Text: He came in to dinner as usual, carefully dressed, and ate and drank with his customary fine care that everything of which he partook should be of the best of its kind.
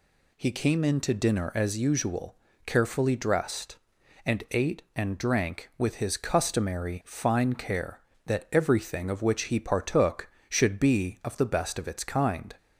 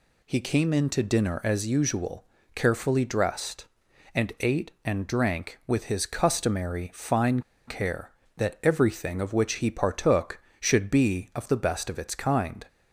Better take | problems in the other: first | pauses between "fine" and "care"; slight; at 7.4 s; 0.26 s long

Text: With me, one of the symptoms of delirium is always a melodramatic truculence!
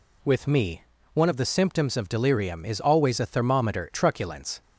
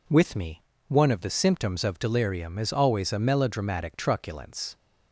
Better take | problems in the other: second | says "thermometer" for "melodramatic"; at 3.2 s

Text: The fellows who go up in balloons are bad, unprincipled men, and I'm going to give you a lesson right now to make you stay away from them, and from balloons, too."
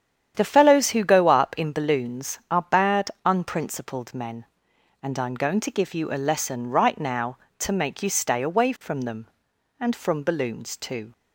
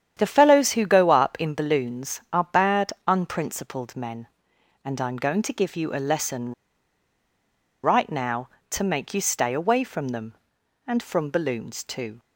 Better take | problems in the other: first | starts louder than the rest; strong; until 1.1 s; 9.5 dB; strong in the first // pauses between "lesson" and "right"; strong; at 6.5 s; 1.3 s long

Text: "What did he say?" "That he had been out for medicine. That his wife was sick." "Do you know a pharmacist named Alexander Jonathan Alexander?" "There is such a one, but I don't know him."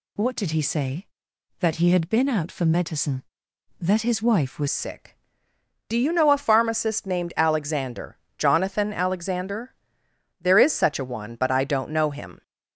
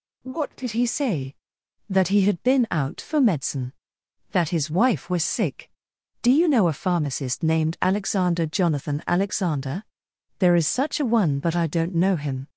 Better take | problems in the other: second | changes voice at "sick"; from 4.7 s on; 7.7 s long // pauses between "Alexander" and "Jonathan"; slight; at 8.1 s; 0.18 s long

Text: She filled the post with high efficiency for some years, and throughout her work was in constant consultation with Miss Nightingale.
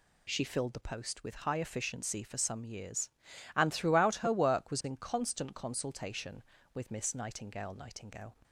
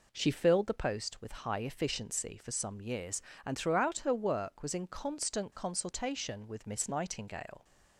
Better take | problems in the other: second | says "Nightingale" twice; at 7.7 s

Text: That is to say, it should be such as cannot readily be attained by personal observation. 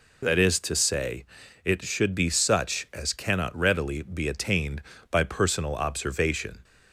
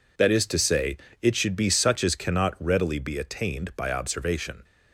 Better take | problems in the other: first | skips "personal"; at 3.9 s

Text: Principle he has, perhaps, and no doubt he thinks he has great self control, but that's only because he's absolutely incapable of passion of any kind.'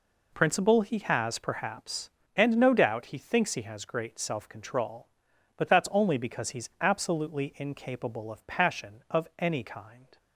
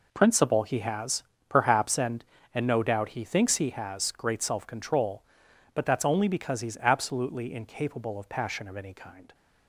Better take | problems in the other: first | says "and" twice; at 2.5 s

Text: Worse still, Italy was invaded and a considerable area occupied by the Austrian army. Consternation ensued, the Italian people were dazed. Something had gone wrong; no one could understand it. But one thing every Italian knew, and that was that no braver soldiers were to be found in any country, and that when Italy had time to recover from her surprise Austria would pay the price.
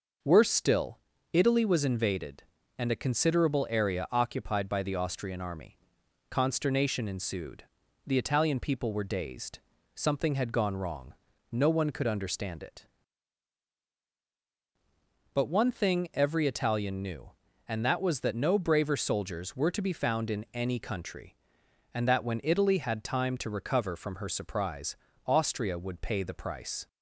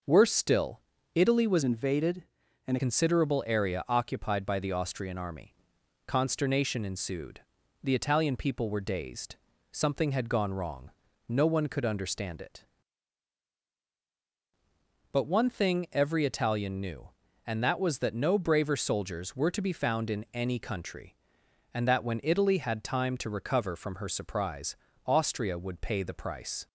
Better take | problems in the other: first | starts louder than the rest; noticeable; until 1.3 s; 6 dB // changes voice from "invaded" to "a"; from 1.6 to 2.8 s; 1.2 s long // pauses between "surprise" and "Austria"; slight; at 24.7 s; 0.32 s long; slight in the first

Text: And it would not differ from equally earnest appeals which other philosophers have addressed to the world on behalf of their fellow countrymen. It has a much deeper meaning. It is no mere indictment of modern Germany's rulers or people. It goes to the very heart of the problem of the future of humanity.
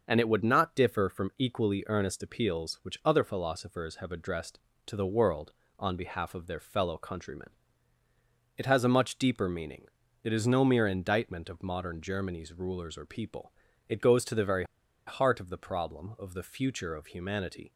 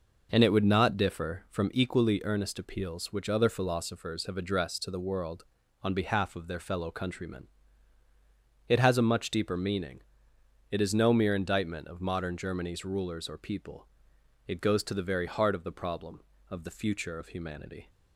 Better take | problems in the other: second | starts louder than the rest; until 1.0 s; 6.5 dB // pauses between "very" and "heart"; at 14.6 s; 0.43 s long

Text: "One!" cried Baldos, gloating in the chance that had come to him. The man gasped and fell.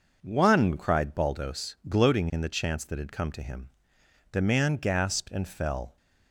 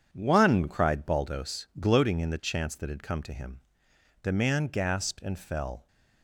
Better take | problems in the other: first | gets quieter; strong; throughout; 9 dB

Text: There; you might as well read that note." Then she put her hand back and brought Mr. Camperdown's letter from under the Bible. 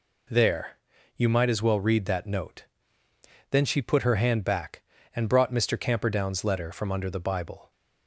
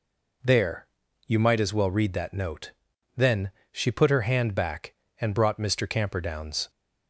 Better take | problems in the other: first | pauses between "Then" and "she"; slight; at 3.4 s; 0.22 s long // stops before "letter from under the Bible"; at 6.6 s

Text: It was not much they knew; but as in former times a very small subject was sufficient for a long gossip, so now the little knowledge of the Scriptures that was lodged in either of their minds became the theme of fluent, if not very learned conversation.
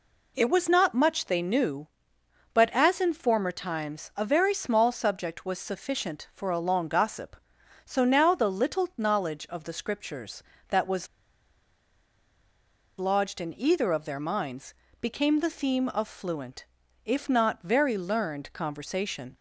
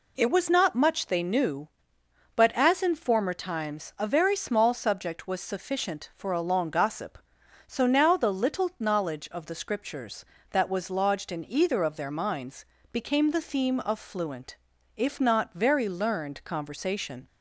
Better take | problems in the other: second | pauses between "was" and "lodged"; strong; at 11.0 s; 1.9 s long // pauses between "minds" and "became"; slight; at 14.7 s; 0.26 s long; slight in the second

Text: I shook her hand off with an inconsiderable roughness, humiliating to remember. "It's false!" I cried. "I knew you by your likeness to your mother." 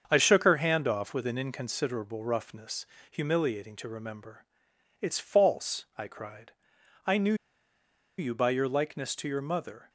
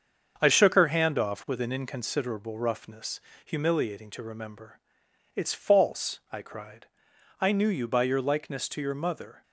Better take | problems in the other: second | starts louder than the rest; until 1.0 s; 7 dB; also in the second // pauses between "knew" and "you"; noticeable; at 7.3 s; 0.84 s long

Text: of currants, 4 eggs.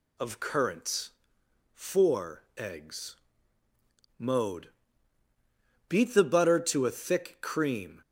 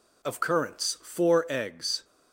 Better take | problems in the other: second | goes on to say "Mode Beat the butter to a thick cream"; strong; from 4.1 s on; 3.8 s long

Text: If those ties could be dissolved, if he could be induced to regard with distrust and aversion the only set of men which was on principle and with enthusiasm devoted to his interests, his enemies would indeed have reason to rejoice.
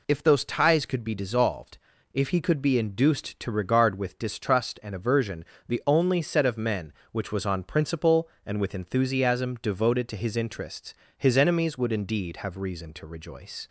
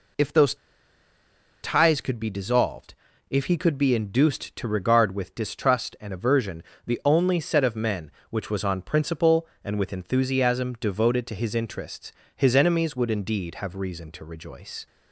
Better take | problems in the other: first | pauses between "those" and "ties"; at 0.5 s; 1.0 s long // pauses between "aversion" and "the"; slight; at 6.6 s; 0.22 s long; slight in the first

